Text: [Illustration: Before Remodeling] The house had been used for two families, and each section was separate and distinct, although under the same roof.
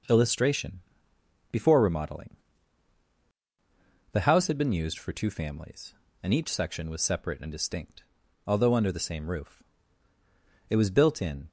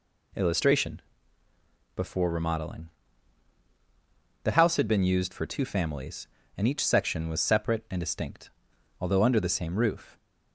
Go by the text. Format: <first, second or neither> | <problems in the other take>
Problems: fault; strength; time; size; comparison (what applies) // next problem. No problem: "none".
second | pauses between "Remodeling" and "The"; strong; at 2.3 s; 1.7 s long; strong in the second // goes on to say "It was built in"; noticeable; from 10.6 s on; 0.82 s long